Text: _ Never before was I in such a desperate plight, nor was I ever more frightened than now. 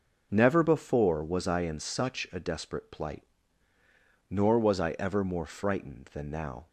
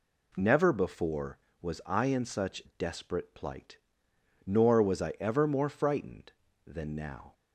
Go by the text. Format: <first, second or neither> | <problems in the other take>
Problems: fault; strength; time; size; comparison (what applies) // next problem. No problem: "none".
first | skips "a"; at 2.6 s